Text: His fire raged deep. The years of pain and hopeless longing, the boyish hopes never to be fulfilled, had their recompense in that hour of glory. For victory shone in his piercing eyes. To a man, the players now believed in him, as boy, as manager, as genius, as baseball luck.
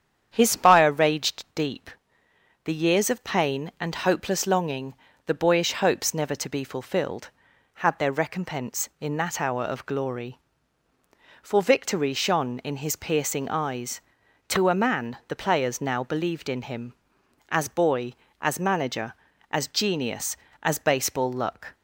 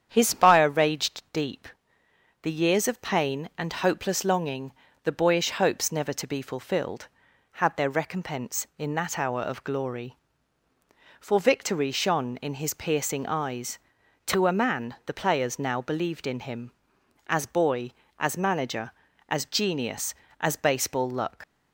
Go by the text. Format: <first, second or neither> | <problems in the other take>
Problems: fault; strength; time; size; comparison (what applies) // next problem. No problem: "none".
first | starts louder than the rest; strong; until 1.1 s; 8.5 dB; strong in the first // leaves "luck" unfinished; at 21.4 s; 80 ms